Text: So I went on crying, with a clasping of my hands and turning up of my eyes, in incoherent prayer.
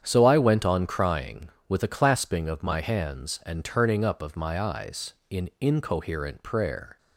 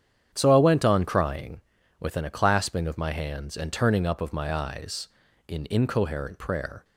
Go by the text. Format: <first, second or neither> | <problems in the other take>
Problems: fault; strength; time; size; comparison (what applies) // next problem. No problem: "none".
first | starts louder than the rest; strong; until 1.3 s; 9 dB; strong in the first // says "within" for "with"; at 2.0 s